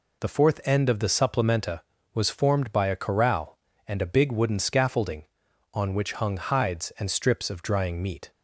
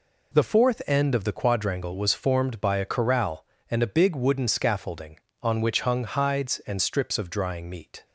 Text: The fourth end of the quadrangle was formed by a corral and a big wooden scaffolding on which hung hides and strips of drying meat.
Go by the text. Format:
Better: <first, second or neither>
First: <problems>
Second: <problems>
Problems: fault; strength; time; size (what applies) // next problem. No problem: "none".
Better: second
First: says "supplementa" for "quadrangle"; at 1.0 s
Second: none